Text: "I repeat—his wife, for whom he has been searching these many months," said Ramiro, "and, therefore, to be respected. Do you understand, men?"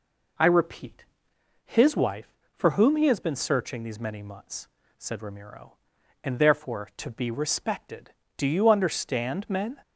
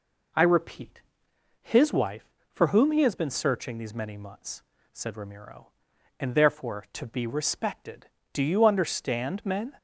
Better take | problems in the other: neither | none

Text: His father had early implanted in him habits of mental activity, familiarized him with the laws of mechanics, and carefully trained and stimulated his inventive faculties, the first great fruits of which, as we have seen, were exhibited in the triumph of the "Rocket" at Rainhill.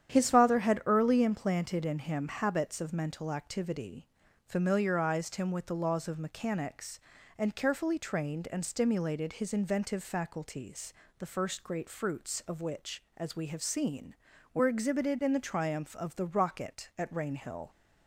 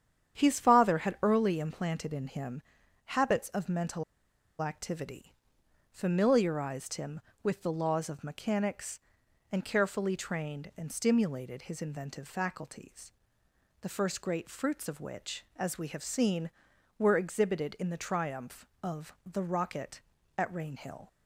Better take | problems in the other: first | starts louder than the rest; strong; until 1.4 s; 9 dB; strong in the first // pauses between "him" and "habits"; noticeable; at 2.6 s; 0.46 s long // pauses between "mental" and "activity"; noticeable; at 4.0 s; 0.57 s long

